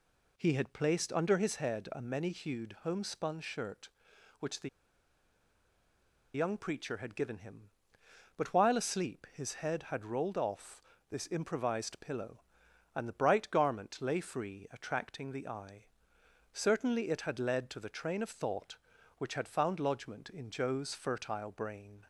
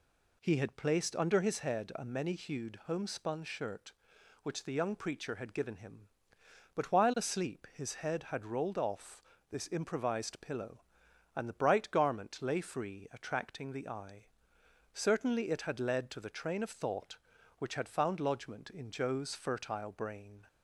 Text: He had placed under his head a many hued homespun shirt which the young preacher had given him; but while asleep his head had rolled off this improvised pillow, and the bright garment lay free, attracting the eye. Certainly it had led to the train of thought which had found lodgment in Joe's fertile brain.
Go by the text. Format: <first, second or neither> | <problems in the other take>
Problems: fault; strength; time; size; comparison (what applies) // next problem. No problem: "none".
second | pauses between "the" and "young"; strong; at 4.6 s; 1.6 s long // pauses between "off" and "this"; slight; at 10.8 s; 0.30 s long; slight in the second